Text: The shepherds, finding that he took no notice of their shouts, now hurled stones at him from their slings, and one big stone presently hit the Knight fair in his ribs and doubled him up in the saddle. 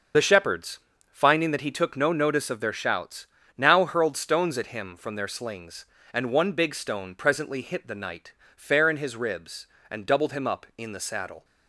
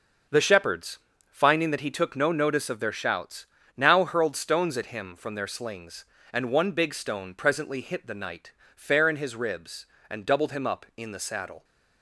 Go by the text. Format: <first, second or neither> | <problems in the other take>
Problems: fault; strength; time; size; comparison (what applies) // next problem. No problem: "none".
second | loses the start of "The"; at 0.1 s; 45 ms // starts louder than the rest; until 1.4 s; 6.5 dB; also in the second // pauses between "Knight" and "fair"; slight; at 8.3 s; 0.24 s long; slight in the second